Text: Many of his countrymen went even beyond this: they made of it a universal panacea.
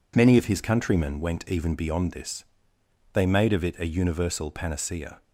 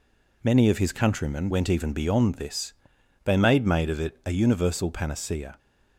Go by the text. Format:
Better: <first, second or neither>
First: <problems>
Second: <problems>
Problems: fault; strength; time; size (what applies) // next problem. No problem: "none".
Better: first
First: none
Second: says "made" twice; at 3.6 s